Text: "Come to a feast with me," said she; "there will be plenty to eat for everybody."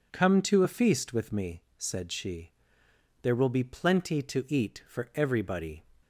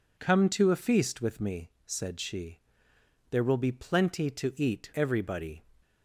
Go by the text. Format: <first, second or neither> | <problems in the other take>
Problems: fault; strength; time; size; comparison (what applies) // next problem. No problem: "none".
first | skips "for"; at 4.9 s